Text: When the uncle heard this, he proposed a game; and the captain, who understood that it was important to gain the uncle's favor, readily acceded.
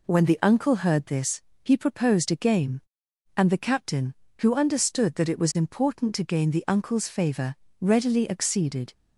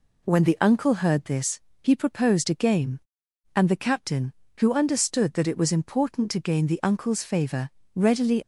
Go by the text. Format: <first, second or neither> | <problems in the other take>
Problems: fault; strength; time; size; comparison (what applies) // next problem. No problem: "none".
first | stops before "acceded"; at 8.4 s